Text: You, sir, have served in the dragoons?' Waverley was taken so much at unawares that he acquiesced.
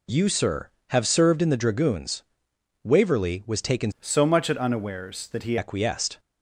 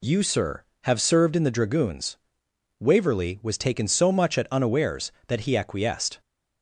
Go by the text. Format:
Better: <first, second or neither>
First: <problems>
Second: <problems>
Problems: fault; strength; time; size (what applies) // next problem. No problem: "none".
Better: second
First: changes voice from "so" to "he"; from 3.9 to 5.5 s; 1.6 s long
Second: none